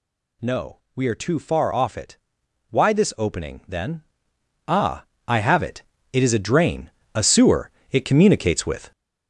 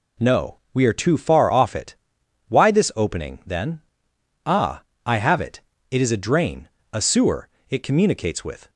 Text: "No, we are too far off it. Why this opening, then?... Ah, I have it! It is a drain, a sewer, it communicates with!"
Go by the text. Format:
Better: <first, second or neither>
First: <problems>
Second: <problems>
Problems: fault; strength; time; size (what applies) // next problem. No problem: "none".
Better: second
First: gets louder; noticeable; throughout; 6 dB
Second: none